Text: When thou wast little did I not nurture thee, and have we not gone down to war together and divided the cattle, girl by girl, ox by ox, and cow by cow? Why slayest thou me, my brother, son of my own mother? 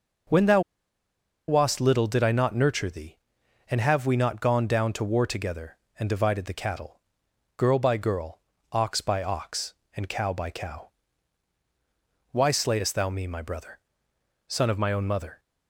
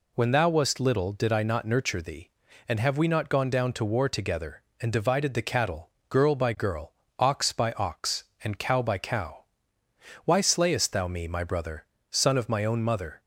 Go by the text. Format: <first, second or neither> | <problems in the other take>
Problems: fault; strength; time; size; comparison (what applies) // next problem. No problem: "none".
second | starts louder than the rest; noticeable; until 2.1 s; 6 dB // pauses between "thou" and "wast"; noticeable; at 0.6 s; 0.88 s long